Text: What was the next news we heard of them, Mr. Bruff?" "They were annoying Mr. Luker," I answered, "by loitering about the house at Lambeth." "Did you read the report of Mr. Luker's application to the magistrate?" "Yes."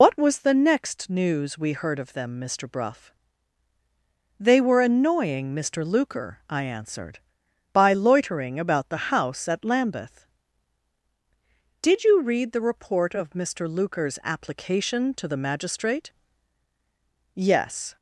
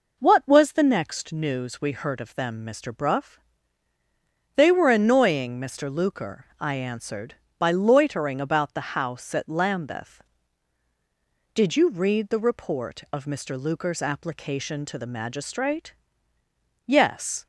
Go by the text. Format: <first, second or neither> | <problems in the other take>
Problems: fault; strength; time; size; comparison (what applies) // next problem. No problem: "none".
second | loses the start of "What"; at 0.0 s; 80 ms